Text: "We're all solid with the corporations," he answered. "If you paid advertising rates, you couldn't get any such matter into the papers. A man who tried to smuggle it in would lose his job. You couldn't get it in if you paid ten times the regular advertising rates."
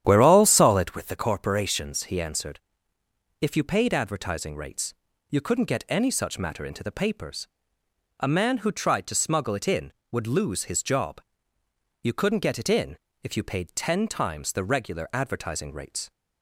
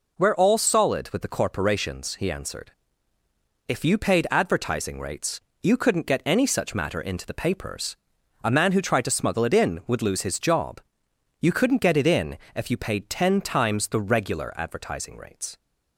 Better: second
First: starts louder than the rest; strong; until 1.2 s; 10 dB // pauses between "in" and "if"; slight; at 12.9 s; 0.26 s long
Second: pauses between "in" and "if"; slight; at 12.3 s; 0.16 s long

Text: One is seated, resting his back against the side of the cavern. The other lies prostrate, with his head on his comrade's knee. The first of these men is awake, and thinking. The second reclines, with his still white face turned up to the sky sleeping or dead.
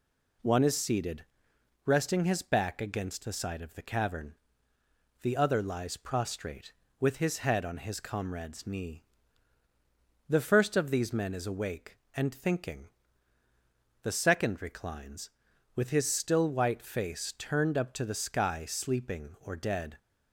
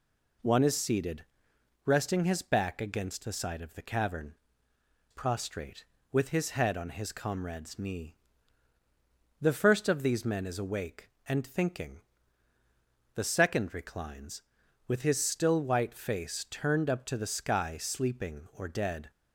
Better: first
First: none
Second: skips "The other lies"; at 4.7 s

